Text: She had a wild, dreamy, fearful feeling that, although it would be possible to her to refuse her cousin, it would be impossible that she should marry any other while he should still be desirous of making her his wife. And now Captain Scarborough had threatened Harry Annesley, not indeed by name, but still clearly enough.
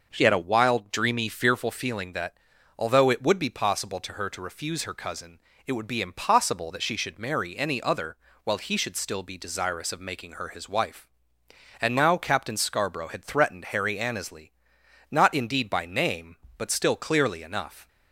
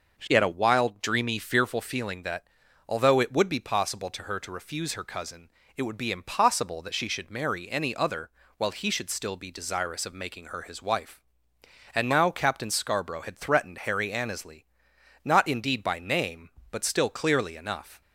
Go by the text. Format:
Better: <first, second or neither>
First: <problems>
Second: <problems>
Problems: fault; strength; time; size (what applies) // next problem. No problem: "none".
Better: neither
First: pauses between "other" and "while"; slight; at 8.1 s; 0.26 s long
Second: pauses between "other" and "while"; slight; at 8.3 s; 0.26 s long